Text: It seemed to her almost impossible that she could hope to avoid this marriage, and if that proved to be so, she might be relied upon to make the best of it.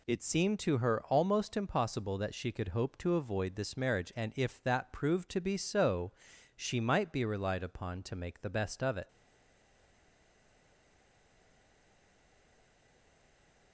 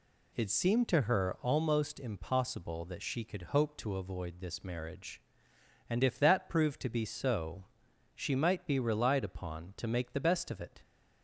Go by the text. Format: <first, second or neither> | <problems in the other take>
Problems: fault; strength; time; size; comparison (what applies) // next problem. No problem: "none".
second | stays silent after the last word; strong; from 9.0 s on; 4.7 s long